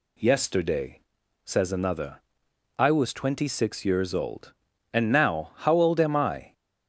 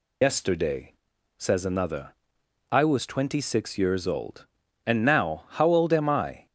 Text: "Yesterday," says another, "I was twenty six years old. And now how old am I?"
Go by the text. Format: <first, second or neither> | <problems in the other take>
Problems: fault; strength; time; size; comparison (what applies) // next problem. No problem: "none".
first | loses the start of "Yesterday"; at 0.2 s; 100 ms